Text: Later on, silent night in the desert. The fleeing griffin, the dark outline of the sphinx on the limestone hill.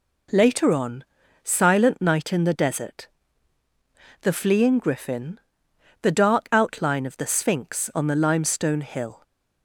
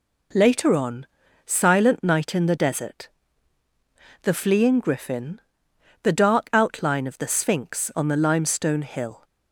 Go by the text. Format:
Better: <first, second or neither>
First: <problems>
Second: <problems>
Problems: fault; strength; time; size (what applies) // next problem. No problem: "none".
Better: neither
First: none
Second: none